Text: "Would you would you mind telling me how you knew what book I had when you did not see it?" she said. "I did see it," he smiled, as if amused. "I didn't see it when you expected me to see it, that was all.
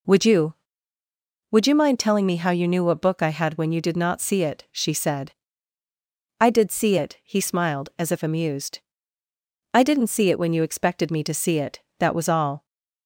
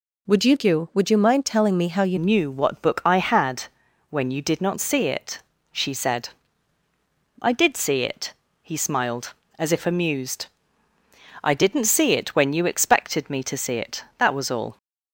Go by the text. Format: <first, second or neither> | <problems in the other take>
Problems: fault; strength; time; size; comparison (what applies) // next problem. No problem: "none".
first | changes voice at "knew"; from 2.1 s on; 12.6 s long // pauses between "had" and "when"; noticeable; at 3.6 s; 0.48 s long